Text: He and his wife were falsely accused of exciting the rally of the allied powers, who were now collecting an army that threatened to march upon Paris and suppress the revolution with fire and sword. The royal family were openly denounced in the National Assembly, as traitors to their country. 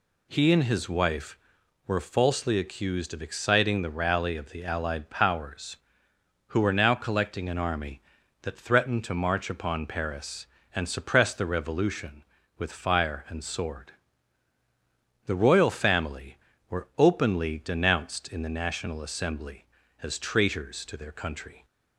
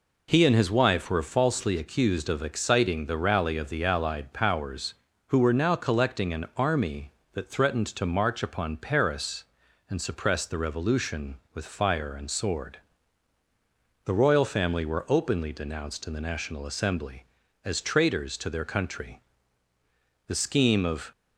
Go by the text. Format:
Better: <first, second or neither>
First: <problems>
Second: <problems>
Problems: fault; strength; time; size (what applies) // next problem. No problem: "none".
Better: first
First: none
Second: goes on to say "The scheme of"; noticeable; from 20.2 s on; 0.84 s long